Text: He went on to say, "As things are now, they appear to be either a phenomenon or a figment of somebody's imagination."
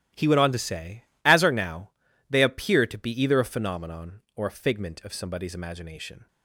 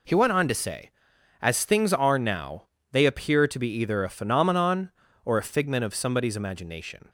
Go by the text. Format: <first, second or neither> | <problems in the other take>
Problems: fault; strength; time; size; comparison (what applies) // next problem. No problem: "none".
second | starts louder than the rest; strong; until 1.3 s; 14 dB // skips "things"; at 1.4 s